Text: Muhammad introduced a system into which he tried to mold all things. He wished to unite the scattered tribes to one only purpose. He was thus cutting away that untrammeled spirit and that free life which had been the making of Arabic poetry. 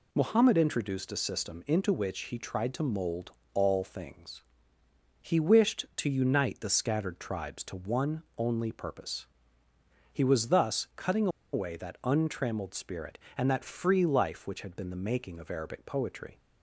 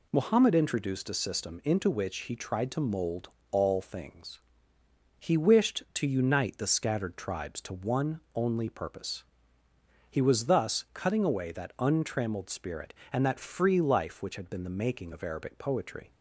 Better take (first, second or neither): second